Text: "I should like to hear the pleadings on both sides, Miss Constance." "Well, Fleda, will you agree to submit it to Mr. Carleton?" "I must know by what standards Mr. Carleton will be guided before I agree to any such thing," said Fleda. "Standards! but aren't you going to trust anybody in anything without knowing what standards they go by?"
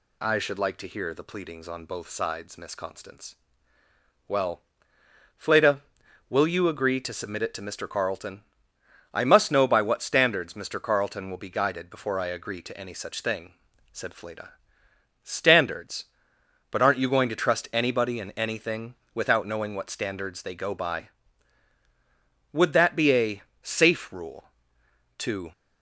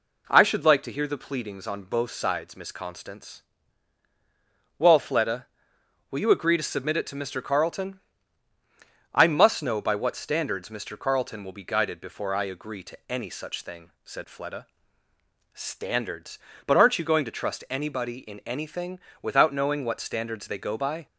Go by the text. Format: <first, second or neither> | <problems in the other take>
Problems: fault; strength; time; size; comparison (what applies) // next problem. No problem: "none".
second | pauses between "anything" and "without"; slight; at 18.9 s; 0.18 s long; slight in the second // goes on to say "Would that be a safe rule to"; strong; from 22.5 s on; 3.0 s long